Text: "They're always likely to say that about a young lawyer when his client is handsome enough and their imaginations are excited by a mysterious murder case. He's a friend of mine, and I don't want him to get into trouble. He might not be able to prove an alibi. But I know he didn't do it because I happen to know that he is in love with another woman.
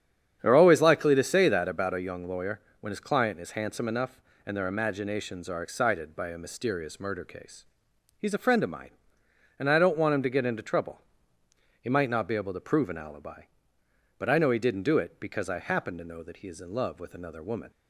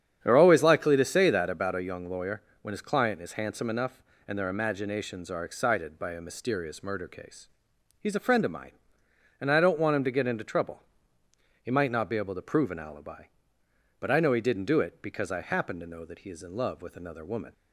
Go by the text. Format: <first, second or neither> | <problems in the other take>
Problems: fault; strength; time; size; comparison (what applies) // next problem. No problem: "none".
neither | starts louder than the rest; strong; the same in both // pauses between "lawyer" and "when"; slight; the same in both